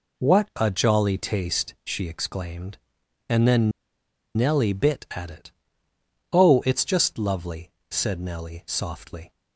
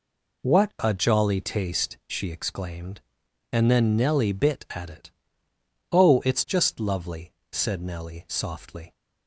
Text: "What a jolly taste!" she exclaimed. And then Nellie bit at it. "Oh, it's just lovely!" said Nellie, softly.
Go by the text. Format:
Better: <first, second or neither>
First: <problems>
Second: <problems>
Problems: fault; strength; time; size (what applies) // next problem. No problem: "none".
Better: second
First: pauses between "then" and "Nellie"; noticeable; at 3.7 s; 0.66 s long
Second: none